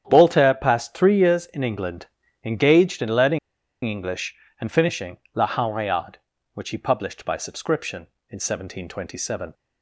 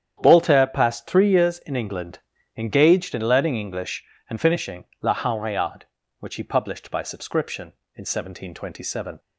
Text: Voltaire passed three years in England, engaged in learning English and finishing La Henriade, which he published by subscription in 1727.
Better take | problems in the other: second | starts louder than the rest; strong; until 1.0 s; 9 dB; strong in the second // pauses between "learning" and "English"; noticeable; at 3.3 s; 0.46 s long // pauses between "finishing" and "La"; slight; at 5.1 s; 0.18 s long; slight in the second

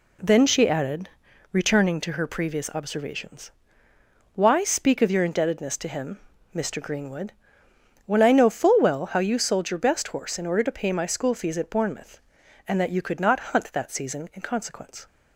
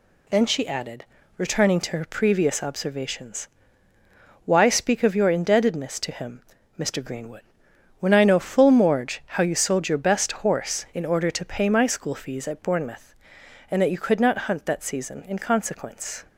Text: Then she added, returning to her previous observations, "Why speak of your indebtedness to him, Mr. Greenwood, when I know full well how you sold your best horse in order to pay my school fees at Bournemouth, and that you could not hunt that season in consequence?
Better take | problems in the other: first | says "morge" for "well"; at 8.6 s

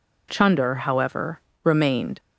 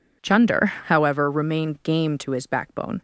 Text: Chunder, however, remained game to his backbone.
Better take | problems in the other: second | stops before "game to his backbone"; at 2.1 s

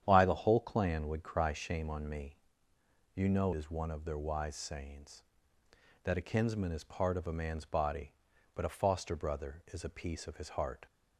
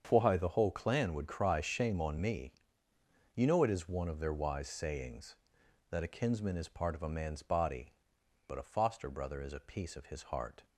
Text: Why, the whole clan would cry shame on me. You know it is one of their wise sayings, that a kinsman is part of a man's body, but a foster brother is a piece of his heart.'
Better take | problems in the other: second | starts louder than the rest; strong; until 1.0 s; 9.5 dB; strong in the second // skips "it"; at 3.5 s

